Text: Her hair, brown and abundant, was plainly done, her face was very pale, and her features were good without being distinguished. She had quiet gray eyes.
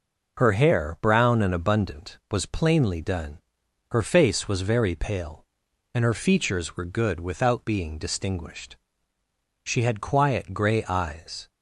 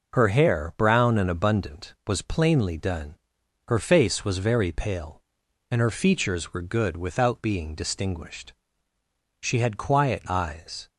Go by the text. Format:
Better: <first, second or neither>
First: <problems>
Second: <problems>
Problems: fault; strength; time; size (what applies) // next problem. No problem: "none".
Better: first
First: none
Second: skips "gray"; at 10.2 s